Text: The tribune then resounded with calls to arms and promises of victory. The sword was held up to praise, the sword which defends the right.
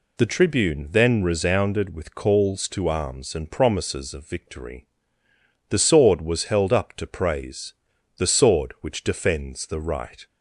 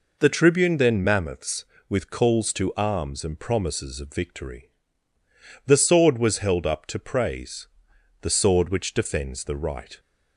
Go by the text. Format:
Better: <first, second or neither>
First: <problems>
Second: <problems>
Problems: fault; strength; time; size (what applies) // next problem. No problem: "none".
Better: first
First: none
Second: says "mammoths" for "resounded"; at 1.0 s